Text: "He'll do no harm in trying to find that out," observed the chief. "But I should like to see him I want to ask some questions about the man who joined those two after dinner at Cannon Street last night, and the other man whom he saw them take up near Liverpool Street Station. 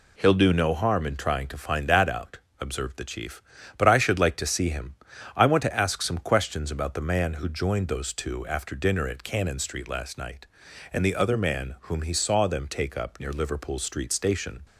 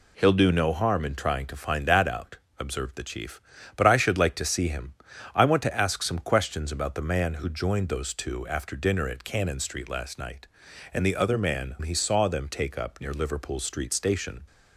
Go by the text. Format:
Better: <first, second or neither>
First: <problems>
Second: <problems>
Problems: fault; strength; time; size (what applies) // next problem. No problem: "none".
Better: first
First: pauses between "him" and "I"; at 4.9 s; 0.40 s long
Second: pauses between "him" and "I"; at 4.9 s; 0.40 s long // skips "whom"; at 11.7 s